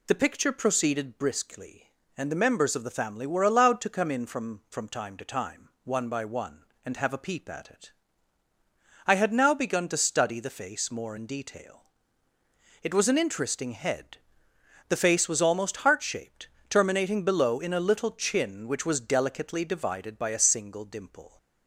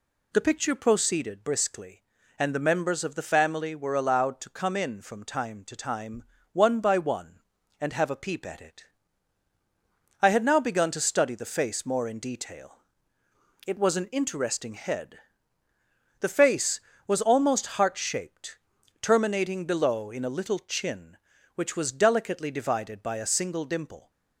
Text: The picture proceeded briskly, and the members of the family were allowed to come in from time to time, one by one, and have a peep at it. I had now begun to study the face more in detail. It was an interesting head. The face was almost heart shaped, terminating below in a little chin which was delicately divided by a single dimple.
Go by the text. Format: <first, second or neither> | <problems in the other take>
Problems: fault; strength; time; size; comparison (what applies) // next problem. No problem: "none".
second | says "from" twice; at 4.6 s